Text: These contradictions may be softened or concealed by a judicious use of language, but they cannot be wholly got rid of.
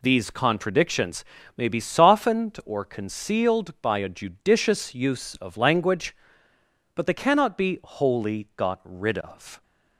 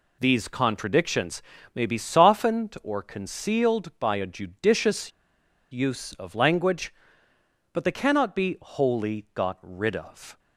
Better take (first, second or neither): first